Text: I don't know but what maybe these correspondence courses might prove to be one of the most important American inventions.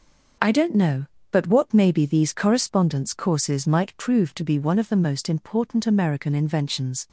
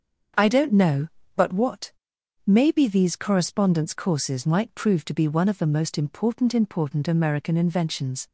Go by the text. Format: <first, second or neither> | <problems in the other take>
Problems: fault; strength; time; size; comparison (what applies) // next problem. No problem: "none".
first | starts louder than the rest; strong; until 1.6 s; 7 dB; also in the first // pauses between "what" and "maybe"; noticeable; at 1.9 s; 0.52 s long // says "important" twice; at 6.5 s